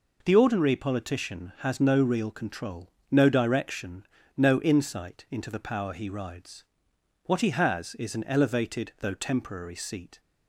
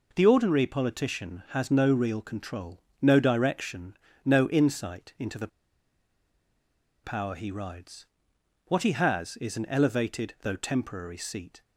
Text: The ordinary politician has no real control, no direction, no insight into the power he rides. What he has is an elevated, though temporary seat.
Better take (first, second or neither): first